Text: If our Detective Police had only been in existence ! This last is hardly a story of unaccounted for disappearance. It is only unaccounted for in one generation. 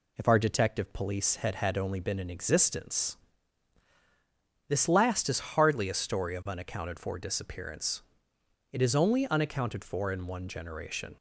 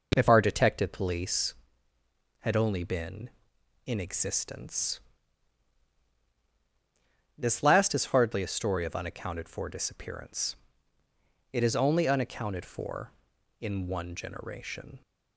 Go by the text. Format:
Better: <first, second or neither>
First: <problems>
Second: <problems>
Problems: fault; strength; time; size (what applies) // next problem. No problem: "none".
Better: second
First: says "had" twice; at 1.5 s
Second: none